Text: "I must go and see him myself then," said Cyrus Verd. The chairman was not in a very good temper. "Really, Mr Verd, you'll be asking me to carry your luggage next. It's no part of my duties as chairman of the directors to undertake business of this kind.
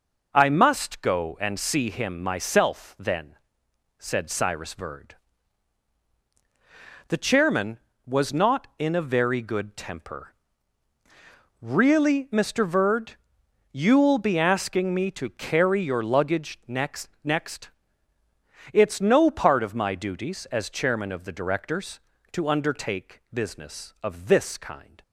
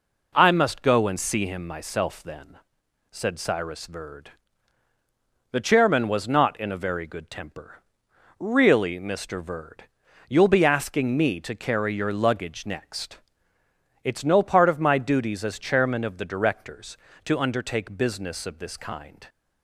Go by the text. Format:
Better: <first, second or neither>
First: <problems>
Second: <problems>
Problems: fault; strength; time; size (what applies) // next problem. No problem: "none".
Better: second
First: says "next" twice; at 17.2 s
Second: none